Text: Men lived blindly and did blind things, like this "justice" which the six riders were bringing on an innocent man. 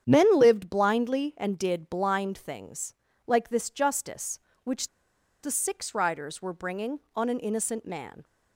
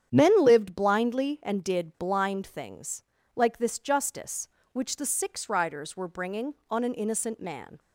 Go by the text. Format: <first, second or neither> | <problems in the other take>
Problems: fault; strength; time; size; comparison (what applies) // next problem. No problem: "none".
second | starts louder than the rest; strong; until 1.0 s; 9 dB; strong in the second // pauses between "which" and "the"; noticeable; at 4.8 s; 0.56 s long